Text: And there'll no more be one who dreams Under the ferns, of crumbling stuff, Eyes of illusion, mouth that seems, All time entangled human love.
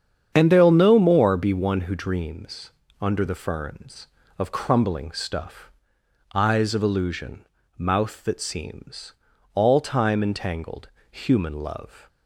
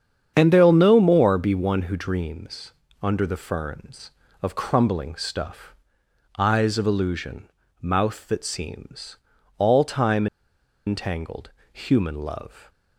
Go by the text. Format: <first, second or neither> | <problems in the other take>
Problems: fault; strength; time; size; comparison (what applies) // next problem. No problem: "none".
first | starts louder than the rest; strong; until 1.3 s; 8 dB; strong in the first // pauses between "dreams" and "Under"; slight; at 2.7 s; 0.30 s long; slight in the first // pauses between "time" and "entangled"; noticeable; at 10.2 s; 0.60 s long // pauses between "entangled" and "human"; slight; at 11.4 s; 0.22 s long; slight in the first